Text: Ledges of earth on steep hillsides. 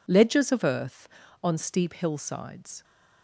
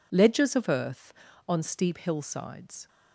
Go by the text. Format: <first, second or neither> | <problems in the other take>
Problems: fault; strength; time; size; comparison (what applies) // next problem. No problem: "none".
neither | none